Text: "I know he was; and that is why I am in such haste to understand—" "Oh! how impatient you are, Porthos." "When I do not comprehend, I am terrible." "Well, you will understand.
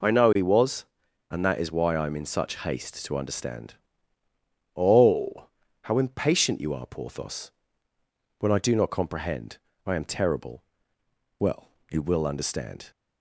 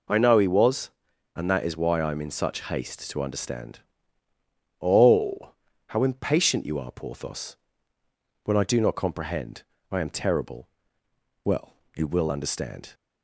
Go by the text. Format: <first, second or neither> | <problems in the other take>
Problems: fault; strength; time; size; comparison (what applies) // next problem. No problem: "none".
neither | none